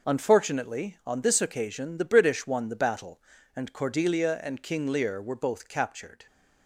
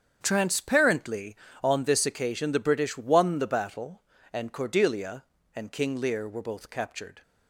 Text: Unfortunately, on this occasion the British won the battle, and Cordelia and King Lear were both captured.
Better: first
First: none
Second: starts louder than the rest; strong; until 1.2 s; 7.5 dB // says "Transparently" for "Unfortunately"; at 0.2 s

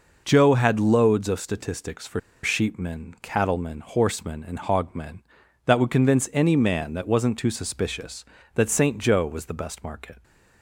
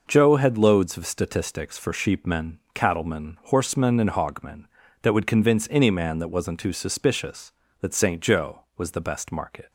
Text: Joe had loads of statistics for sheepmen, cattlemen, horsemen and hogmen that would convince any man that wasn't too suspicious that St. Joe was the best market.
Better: second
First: pauses between "for" and "sheepmen"; slight; at 2.1 s; 0.23 s long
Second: none

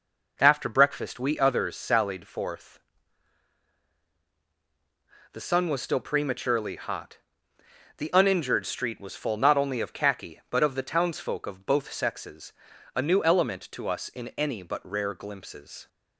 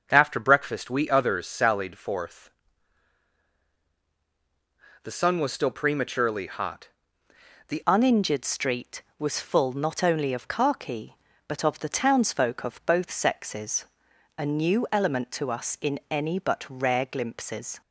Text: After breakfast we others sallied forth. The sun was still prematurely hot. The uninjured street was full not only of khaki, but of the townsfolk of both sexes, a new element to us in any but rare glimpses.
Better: first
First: none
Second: starts louder than the rest; until 1.1 s; 6.5 dB // changes voice at "uninjured"; from 7.8 s on; 10.0 s long

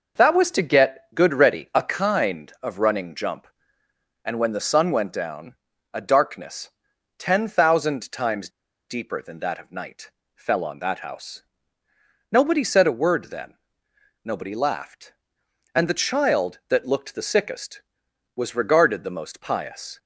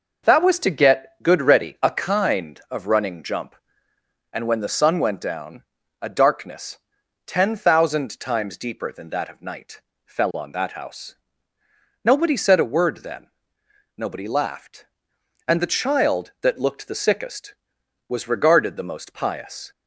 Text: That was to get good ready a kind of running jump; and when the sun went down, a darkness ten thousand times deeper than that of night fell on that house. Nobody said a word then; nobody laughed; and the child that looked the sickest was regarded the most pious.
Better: second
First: pauses between "darkness" and "ten"; noticeable; at 6.7 s; 0.48 s long // pauses between "times" and "deeper"; at 8.4 s; 0.40 s long // pauses between "night" and "fell"; slight; at 10.1 s; 0.24 s long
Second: pauses between "darkness" and "ten"; noticeable; at 6.7 s; 0.48 s long // pauses between "night" and "fell"; slight; at 9.8 s; 0.24 s long

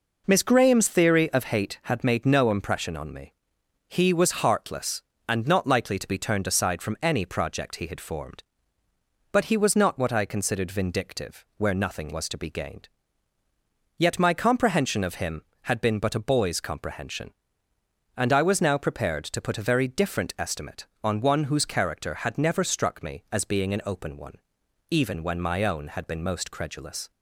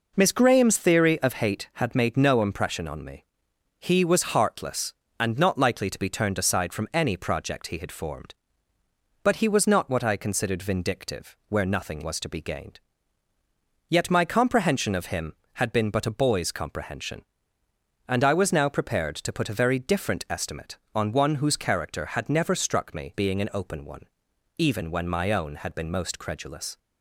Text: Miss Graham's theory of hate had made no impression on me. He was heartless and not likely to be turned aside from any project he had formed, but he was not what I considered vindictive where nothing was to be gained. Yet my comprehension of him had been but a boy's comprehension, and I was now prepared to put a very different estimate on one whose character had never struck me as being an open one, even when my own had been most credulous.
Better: first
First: none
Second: skips "as"; at 23.1 s

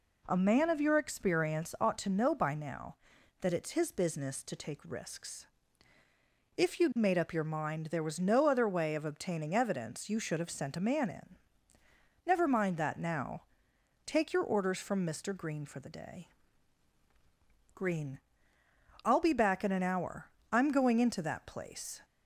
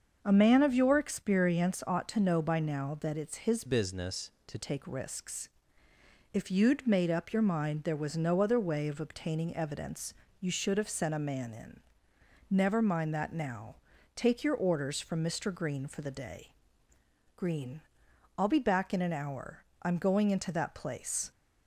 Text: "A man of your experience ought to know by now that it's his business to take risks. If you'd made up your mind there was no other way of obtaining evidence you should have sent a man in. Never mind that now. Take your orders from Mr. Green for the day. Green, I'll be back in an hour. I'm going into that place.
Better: first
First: none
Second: starts louder than the rest; until 1.2 s; 6.5 dB // changes voice from "business" to "to"; from 3.6 to 4.5 s; 0.9 s long // pauses between "evidence" and "you"; slight; at 10.1 s; 0.28 s long

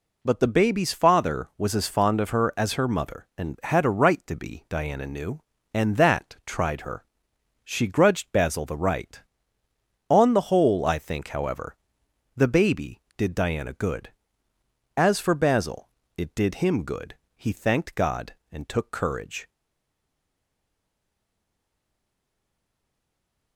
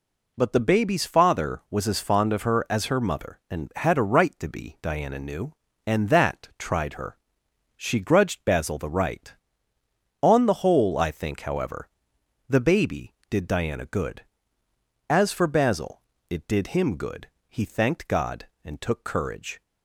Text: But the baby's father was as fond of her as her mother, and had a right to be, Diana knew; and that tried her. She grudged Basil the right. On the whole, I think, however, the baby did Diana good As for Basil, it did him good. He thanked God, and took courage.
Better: second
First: stays silent after the last word; strong; from 19.4 s on; 4.1 s long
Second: none

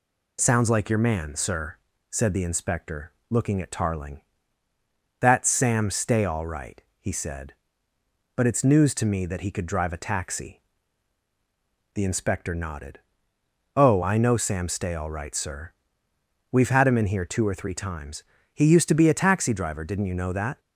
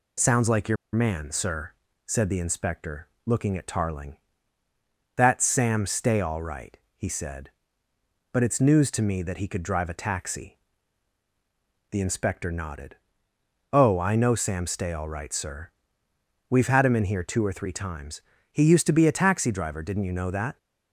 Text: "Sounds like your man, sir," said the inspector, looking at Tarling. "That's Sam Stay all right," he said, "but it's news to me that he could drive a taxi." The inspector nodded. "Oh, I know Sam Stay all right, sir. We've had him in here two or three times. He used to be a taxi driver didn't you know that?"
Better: first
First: none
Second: pauses between "your" and "man"; slight; at 0.7 s; 0.17 s long

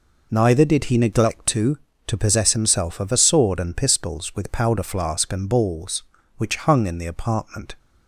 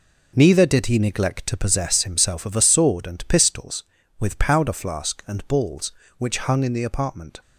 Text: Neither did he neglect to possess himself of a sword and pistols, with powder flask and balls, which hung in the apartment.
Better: second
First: says "to" twice; at 2.0 s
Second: none

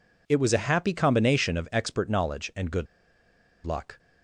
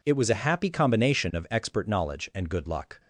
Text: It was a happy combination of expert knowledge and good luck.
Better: second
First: pauses between "good" and "luck"; noticeable; at 2.8 s; 0.79 s long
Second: none

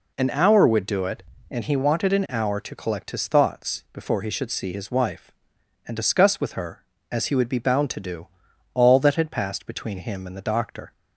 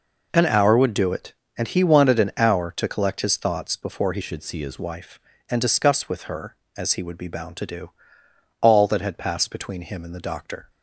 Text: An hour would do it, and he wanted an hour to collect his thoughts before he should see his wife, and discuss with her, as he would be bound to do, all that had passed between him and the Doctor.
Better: first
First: none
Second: changes voice from "should" to "his"; from 4.2 to 4.7 s; 0.5 s long

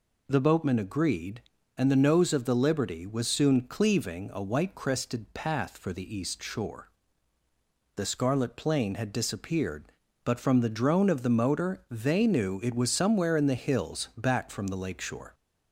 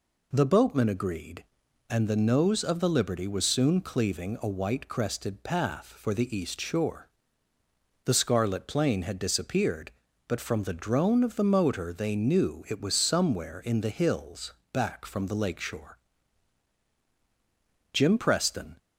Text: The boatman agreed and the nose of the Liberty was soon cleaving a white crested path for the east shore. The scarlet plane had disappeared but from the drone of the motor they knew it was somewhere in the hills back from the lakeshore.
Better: first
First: none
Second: pauses between "hills" and "back"; slight; at 14.5 s; 0.22 s long // goes on to say "Jim Preston"; noticeable; from 17.9 s on; 0.84 s long

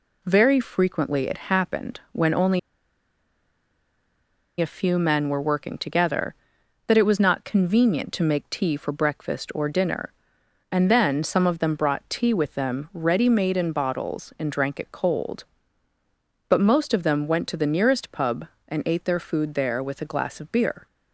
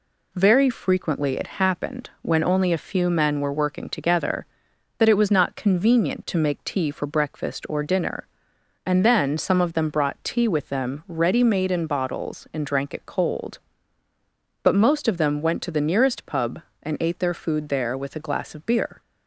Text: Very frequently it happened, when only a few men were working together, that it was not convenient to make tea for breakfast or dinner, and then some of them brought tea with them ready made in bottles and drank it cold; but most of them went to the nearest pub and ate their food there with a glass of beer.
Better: second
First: pauses between "only" and "a"; strong; at 2.5 s; 2.0 s long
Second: none

